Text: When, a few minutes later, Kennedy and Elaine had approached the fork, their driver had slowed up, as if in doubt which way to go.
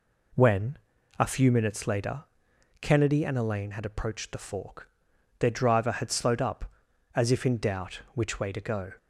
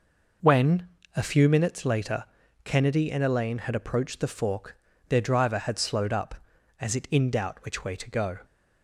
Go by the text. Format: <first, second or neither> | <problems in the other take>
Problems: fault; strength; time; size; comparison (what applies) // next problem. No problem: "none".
first | says "it" for "if"; at 6.9 s